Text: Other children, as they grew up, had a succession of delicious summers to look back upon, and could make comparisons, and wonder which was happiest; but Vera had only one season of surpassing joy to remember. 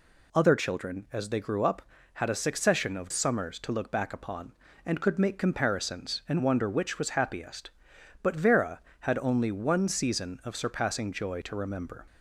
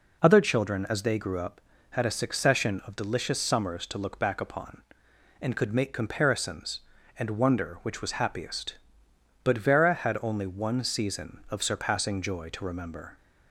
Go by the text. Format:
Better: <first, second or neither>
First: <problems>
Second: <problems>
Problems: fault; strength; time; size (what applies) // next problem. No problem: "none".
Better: second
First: skips "delicious"; at 3.1 s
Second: none